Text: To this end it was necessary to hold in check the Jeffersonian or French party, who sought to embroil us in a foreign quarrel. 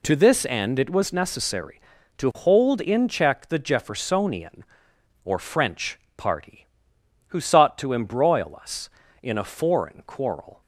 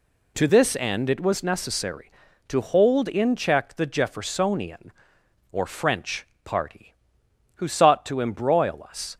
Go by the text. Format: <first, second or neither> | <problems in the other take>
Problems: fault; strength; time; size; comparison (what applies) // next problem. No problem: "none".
first | pauses between "French" and "party"; slight; at 6.2 s; 0.18 s long; slight in the first // stops before "in a foreign quarrel"; at 9.1 s